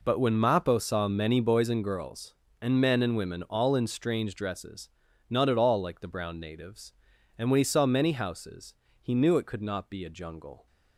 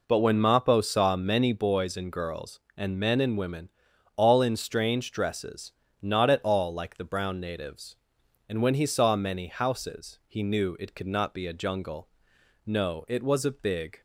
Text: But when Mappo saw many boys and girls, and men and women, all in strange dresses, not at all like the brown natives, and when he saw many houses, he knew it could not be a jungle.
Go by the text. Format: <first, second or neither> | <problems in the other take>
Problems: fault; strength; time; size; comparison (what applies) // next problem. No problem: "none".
first | goes on to say "No it was a big"; from 12.6 s on; 1.3 s long